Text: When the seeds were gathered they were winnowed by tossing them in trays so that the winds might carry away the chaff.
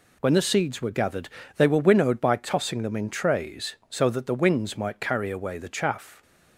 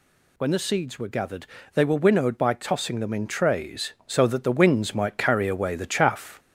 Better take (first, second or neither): first